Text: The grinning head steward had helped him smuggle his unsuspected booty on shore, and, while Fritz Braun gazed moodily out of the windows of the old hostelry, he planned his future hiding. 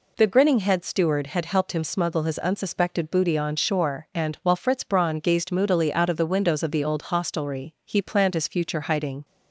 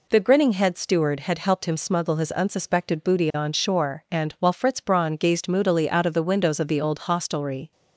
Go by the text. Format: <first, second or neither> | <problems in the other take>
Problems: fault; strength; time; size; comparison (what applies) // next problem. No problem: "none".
first | stops before "he planned his future hiding"; at 7.7 s